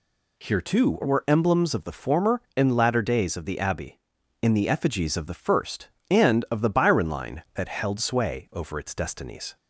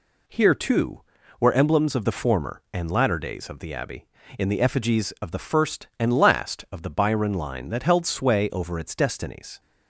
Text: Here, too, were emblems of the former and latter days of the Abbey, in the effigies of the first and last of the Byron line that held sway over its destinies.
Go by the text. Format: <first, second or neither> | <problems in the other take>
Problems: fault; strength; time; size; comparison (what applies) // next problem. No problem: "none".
second | skips "last"; at 6.4 s